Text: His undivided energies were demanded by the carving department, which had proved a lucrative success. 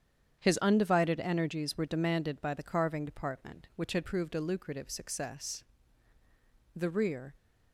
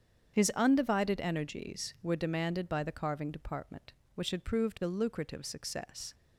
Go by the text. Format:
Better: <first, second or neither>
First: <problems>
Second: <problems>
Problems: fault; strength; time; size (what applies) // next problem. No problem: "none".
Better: second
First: starts louder than the rest; strong; until 1.4 s; 8.5 dB // goes on to say "The rear"; from 6.7 s on; 0.58 s long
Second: starts louder than the rest; strong; until 1.4 s; 8 dB